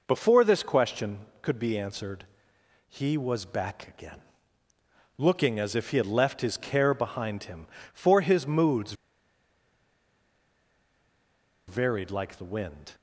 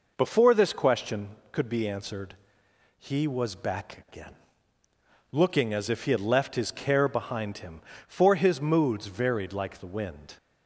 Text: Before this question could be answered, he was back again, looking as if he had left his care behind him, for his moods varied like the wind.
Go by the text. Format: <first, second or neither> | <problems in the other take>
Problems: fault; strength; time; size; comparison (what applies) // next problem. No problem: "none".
second | pauses between "moods" and "varied"; strong; at 8.9 s; 2.7 s long